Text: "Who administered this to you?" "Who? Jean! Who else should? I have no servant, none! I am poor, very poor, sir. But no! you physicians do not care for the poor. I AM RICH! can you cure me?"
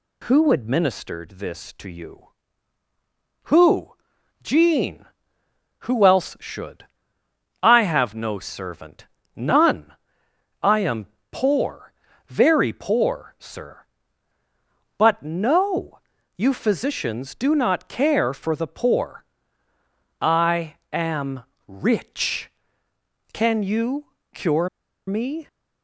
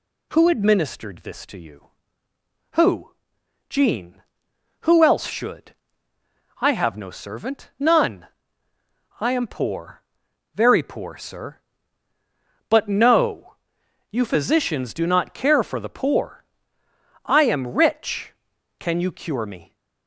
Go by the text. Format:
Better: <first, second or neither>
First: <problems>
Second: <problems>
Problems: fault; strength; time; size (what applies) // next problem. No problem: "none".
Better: second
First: pauses between "am" and "poor"; slight; at 11.0 s; 0.26 s long // pauses between "I" and "AM"; slight; at 20.7 s; 0.16 s long // pauses between "AM" and "RICH"; slight; at 21.4 s; 0.24 s long // pauses between "you" and "cure"; slight; at 24.0 s; 0.28 s long // pauses between "cure" and "me"; at 24.6 s; 0.38 s long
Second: none